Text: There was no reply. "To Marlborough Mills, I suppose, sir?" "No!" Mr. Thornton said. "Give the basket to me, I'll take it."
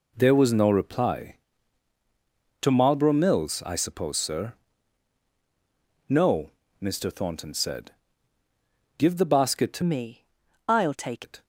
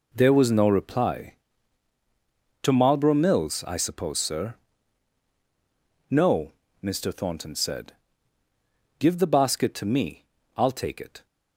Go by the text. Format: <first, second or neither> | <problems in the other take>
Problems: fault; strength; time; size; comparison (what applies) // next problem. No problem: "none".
second | changes voice from "me" to "take"; from 9.8 to 11.2 s; 1.4 s long